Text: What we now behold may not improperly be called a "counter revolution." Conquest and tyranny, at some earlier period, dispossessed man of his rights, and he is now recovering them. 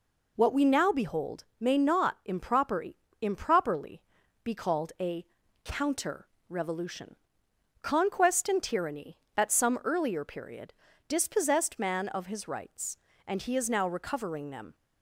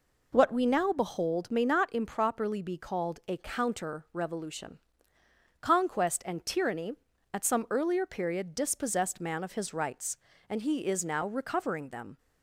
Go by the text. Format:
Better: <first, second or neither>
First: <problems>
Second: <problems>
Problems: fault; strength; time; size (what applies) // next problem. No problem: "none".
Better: second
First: pauses between "behold" and "may"; slight; at 1.4 s; 0.16 s long // says "improperly" twice; at 3.2 s // pauses between "a" and "counter"; at 5.2 s; 0.38 s long // pauses between "counter" and "revolution"; slight; at 6.2 s; 0.22 s long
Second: none